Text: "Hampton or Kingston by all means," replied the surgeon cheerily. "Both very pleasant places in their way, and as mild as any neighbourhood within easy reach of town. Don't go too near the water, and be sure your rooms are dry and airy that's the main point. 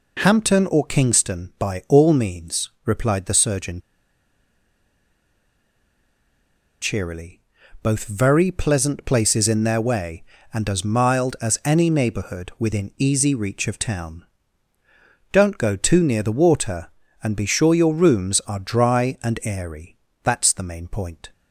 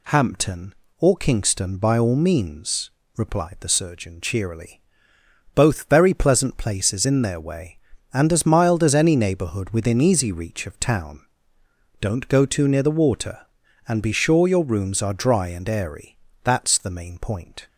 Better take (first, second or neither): second